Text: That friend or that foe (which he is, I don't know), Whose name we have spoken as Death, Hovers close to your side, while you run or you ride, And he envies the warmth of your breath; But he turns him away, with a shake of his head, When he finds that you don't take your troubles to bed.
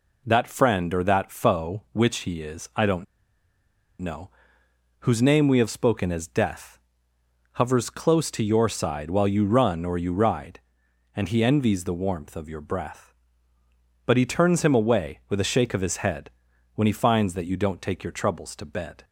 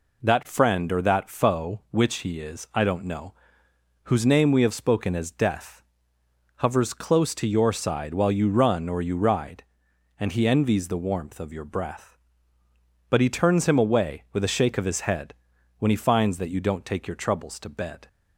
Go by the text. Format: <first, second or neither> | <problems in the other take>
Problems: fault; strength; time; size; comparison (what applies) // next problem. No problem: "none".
second | pauses between "don't" and "know"; noticeable; at 3.0 s; 0.97 s long